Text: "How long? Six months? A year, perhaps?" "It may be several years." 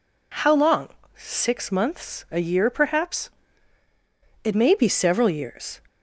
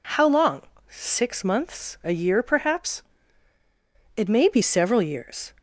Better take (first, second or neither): neither